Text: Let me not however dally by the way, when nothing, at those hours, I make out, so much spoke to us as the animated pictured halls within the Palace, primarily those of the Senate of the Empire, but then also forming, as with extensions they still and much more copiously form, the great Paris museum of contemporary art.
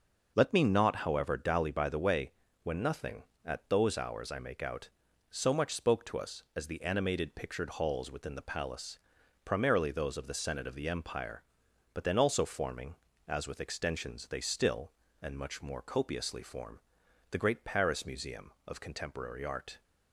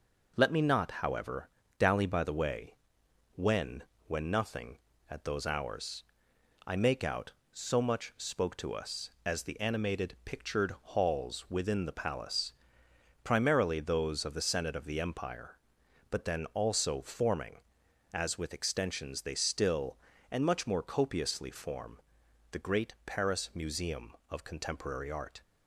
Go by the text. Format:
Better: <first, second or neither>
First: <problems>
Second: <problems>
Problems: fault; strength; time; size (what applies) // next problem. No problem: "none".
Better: first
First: none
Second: pauses between "however" and "dally"; slight; at 1.4 s; 0.30 s long // says "when" twice; at 4.0 s